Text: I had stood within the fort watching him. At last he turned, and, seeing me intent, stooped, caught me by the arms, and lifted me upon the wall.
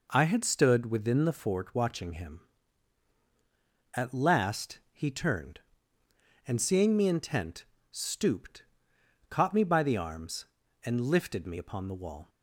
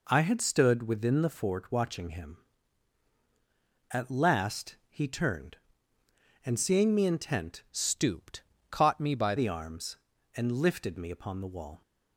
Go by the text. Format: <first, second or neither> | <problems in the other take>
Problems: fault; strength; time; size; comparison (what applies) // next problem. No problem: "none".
first | changes voice from "stooped" to "by"; from 7.7 to 9.3 s; 1.6 s long